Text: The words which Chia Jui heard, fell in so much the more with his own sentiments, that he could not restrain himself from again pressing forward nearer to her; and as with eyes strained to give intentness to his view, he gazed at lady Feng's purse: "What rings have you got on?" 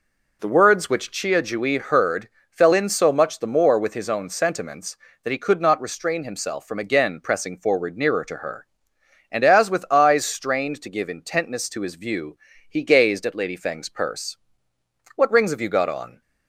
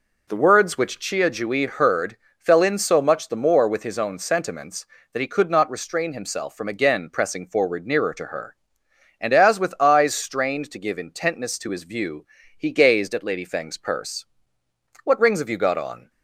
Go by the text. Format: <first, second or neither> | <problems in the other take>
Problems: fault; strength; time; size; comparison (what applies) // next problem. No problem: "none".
neither | none